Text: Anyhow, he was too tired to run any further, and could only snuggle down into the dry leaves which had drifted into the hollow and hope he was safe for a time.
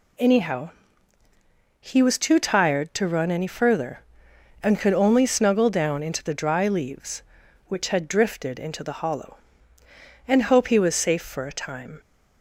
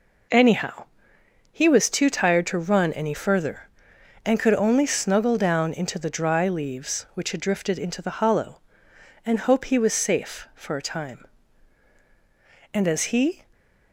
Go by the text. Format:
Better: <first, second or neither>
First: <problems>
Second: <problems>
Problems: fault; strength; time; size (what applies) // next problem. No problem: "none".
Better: first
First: none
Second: goes on to say "And as he"; noticeable; from 12.7 s on; 0.70 s long // stays silent after the last word; slight; from 13.4 s on; 0.5 s long